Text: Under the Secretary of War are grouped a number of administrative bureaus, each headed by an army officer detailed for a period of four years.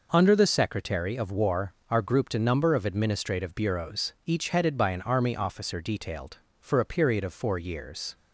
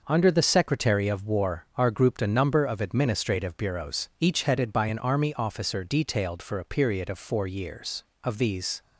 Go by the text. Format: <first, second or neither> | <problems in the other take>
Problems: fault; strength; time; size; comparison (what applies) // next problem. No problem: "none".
first | goes on to say "Of these"; from 8.2 s on; 0.58 s long